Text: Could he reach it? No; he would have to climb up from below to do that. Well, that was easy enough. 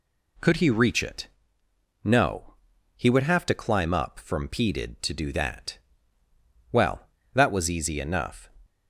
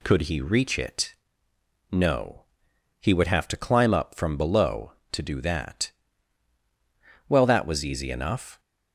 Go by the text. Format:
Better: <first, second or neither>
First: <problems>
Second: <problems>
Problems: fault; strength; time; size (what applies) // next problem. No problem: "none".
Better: second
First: says "peded" for "below"; at 4.4 s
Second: none